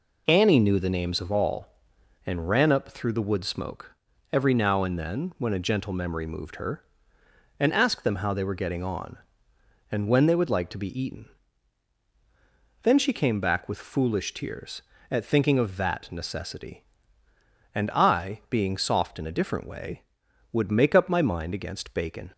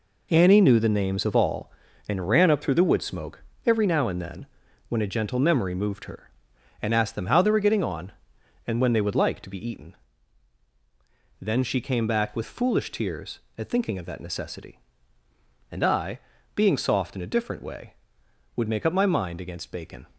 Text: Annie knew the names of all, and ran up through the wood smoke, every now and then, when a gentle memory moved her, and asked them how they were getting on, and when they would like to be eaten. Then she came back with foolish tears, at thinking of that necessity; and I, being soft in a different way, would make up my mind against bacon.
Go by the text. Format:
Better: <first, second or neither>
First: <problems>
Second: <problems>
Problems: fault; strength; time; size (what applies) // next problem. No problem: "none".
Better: first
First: none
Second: gets quieter; strong; throughout; 8 dB